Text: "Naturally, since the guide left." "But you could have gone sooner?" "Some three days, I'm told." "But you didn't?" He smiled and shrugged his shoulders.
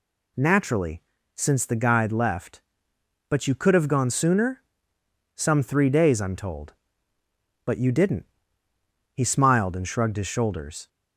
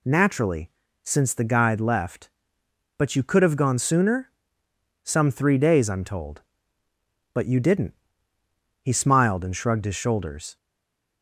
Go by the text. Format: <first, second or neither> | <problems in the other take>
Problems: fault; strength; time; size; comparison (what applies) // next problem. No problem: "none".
first | stays silent after the last word; slight; from 10.5 s on; 0.7 s long